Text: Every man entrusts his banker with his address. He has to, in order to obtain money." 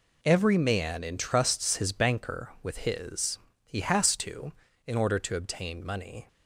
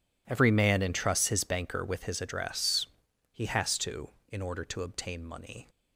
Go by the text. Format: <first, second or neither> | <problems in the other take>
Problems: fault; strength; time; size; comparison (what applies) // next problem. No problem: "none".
second | skips "address"; at 3.5 s